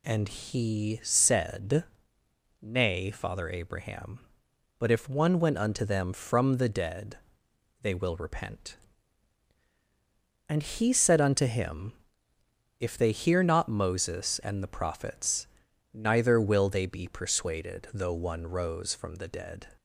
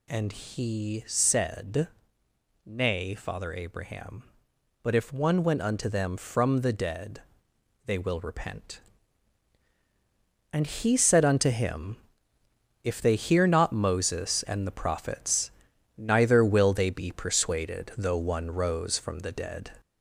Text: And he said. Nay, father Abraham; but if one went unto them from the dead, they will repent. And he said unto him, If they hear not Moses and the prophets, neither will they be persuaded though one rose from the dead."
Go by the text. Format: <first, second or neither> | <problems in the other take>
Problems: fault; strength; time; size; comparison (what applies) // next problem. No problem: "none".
first | gets louder; slight; throughout; 3.5 dB